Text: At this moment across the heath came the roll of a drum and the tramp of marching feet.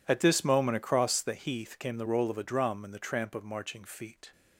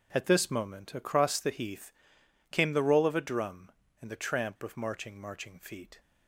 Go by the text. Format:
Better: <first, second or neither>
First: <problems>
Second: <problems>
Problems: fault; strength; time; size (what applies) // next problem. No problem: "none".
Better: first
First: none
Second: pauses between "heath" and "came"; noticeable; at 1.9 s; 0.58 s long // says "marching" twice; at 5.1 s